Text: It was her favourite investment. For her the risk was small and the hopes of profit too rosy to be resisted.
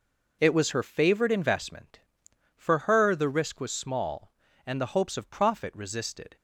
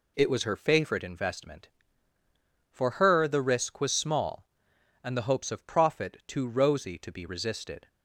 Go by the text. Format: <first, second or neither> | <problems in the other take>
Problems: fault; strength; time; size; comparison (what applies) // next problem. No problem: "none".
second | skips "too rosy to be"; at 5.7 s